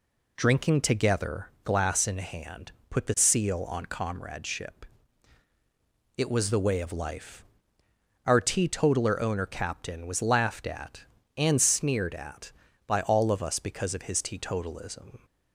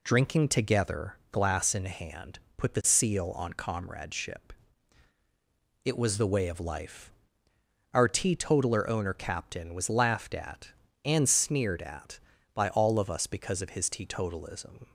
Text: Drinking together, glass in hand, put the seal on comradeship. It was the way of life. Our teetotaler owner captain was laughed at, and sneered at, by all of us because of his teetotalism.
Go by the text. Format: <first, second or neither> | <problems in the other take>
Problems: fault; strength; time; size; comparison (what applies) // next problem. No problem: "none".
neither | none